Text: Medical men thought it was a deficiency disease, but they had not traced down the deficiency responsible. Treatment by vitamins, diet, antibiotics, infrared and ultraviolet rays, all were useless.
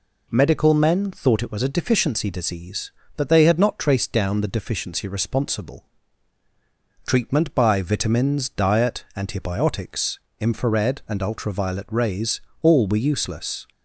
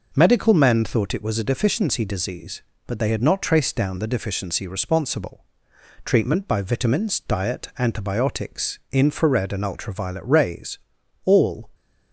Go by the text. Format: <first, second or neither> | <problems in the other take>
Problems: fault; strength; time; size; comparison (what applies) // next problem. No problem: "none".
first | stops before "were useless"; at 11.7 s